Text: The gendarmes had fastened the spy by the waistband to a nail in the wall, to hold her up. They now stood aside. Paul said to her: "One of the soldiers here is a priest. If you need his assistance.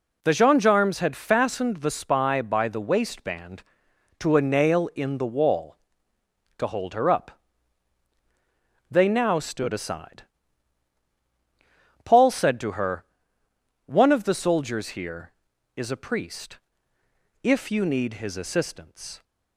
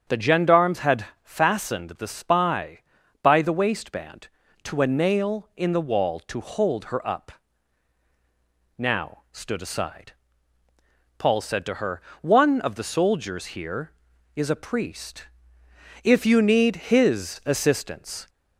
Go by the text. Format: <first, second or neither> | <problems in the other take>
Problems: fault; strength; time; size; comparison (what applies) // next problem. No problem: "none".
first | starts louder than the rest; strong; until 1.2 s; 7.5 dB // pauses between "had" and "fastened"; slight; at 1.0 s; 0.16 s long // skips "They"; at 8.0 s